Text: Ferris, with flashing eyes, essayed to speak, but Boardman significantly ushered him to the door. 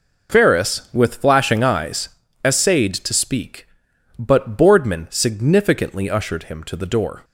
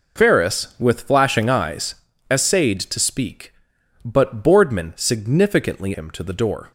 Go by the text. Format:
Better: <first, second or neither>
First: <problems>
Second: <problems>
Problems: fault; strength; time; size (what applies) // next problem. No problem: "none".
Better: first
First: none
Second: skips "ushered"; at 5.9 s